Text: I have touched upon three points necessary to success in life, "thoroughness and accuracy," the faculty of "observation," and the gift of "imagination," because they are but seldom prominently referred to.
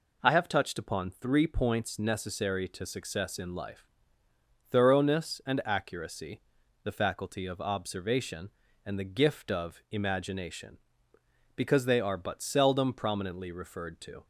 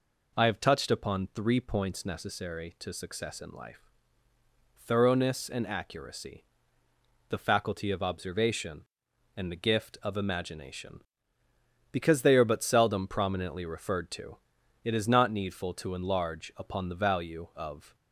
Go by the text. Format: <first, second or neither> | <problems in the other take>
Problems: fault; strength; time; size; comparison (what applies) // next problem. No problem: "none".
first | goes on to say "It is not needful to enlarge upon the value of"; strong; from 14.8 s on; 3.1 s long